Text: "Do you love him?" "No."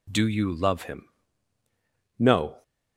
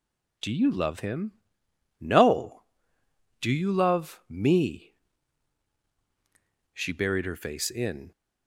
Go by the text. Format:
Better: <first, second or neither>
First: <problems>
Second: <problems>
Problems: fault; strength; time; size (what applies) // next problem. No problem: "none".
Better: first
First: none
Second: goes on to say "Do you love me She buried her face in"; strong; from 3.4 s on; 4.7 s long